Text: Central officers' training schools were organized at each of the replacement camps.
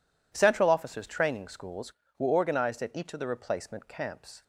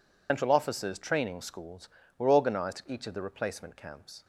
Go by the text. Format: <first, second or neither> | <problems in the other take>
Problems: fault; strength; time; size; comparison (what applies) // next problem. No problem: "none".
first | loses the start of "Central"; at 0.2 s; 125 ms